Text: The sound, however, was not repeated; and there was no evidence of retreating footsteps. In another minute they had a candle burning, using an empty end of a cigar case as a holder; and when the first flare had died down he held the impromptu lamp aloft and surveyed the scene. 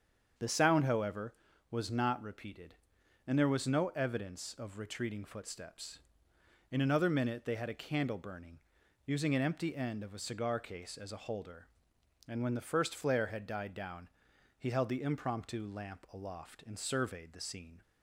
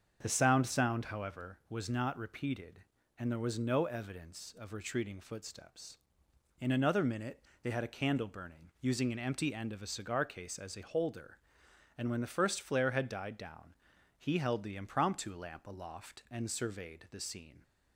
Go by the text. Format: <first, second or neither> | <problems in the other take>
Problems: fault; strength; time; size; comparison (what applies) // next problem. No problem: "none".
first | starts louder than the rest; until 1.2 s; 7 dB; strong in the first // says "sound" twice; at 0.6 s // pauses between "minute" and "they"; slight; at 7.4 s; 0.22 s long // pauses between "down" and "he"; at 13.7 s; 0.42 s long; noticeable in the first